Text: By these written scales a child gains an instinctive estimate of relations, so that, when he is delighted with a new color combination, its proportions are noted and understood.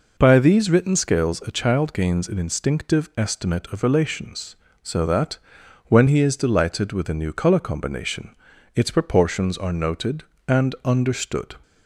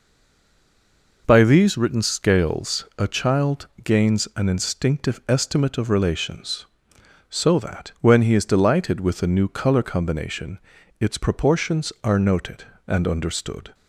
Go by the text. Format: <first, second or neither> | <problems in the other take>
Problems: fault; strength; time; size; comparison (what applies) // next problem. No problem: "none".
first | stays silent before the first word; noticeable; until 1.2 s; 1.2 s long // pauses between "child" and "gains"; slight; at 3.6 s; 0.18 s long